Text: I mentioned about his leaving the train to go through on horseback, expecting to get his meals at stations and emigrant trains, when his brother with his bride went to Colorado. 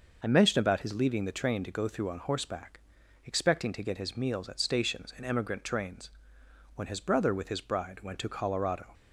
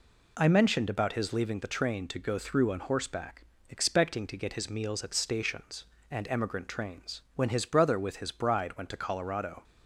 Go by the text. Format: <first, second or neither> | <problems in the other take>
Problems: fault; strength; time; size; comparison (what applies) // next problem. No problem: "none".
neither | none